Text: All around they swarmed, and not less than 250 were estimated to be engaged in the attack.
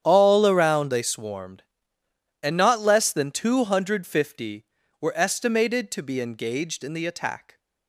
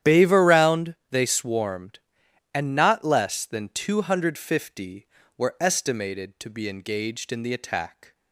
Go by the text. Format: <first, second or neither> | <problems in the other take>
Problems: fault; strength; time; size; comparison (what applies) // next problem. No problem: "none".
first | starts louder than the rest; strong; until 1.1 s; 10.5 dB; strong in the first // says "Bave" for "All"; at 0.0 s